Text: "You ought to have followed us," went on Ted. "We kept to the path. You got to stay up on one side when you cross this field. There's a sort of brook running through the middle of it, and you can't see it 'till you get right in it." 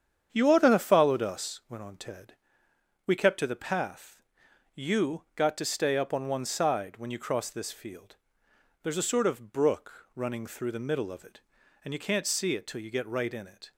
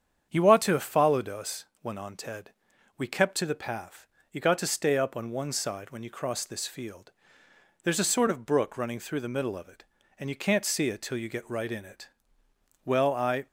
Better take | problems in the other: first | starts louder than the rest; strong; until 1.3 s; 8 dB; strong in the first // goes on to say "Well I"; noticeable; from 12.8 s on; 0.62 s long

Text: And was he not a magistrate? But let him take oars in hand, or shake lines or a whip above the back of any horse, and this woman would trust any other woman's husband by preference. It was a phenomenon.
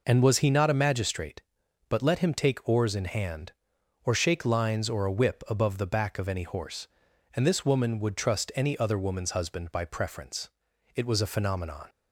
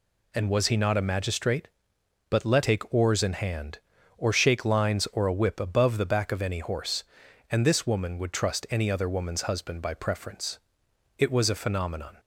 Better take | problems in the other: first | skips "him"; at 2.6 s

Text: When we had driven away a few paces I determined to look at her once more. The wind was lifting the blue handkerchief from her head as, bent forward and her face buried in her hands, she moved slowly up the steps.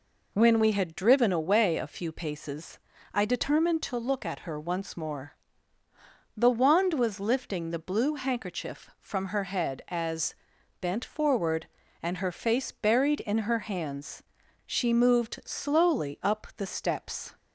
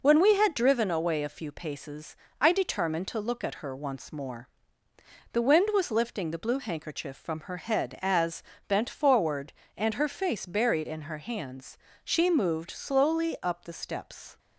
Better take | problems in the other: second | pauses between "paces" and "I"; slight; at 2.7 s; 0.34 s long; slight in the second // says "wand" for "wind"; at 6.4 s

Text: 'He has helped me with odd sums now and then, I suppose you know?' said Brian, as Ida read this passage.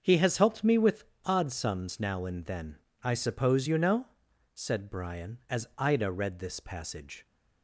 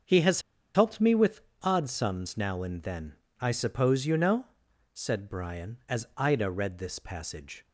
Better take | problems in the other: first | starts louder than the rest; until 1.3 s; 6.5 dB; also in the first // pauses between "has" and "helped"; slight; at 0.4 s; 0.33 s long // pauses between "with" and "odd"; slight; at 1.4 s; 0.22 s long; slight in the first

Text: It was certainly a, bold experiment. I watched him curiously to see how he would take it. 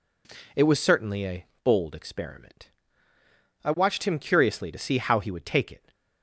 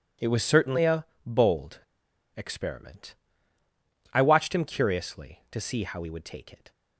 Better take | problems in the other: first | pauses between "bold" and "experiment"; noticeable; at 1.7 s; 0.55 s long

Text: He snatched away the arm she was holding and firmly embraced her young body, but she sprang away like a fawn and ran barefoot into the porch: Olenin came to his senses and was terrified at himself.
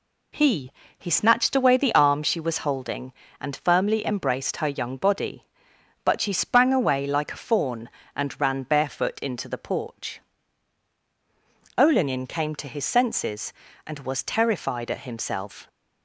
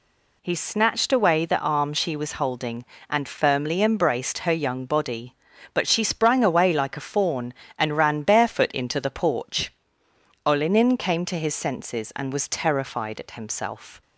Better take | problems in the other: second | says "He" twice; at 0.9 s

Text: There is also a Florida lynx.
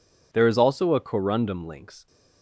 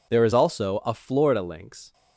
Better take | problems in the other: second | says "Corundum" for "Florida"; at 1.0 s

